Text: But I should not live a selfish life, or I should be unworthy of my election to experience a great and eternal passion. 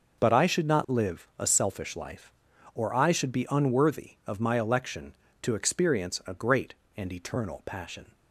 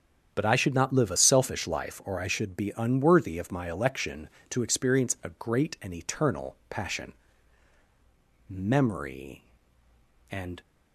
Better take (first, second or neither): first